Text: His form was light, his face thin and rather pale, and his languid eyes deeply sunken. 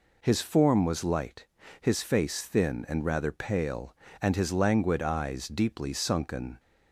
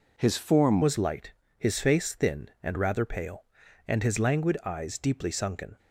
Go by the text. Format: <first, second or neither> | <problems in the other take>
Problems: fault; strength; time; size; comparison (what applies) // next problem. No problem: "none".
first | changes voice at "was"; from 0.8 s on; 4.9 s long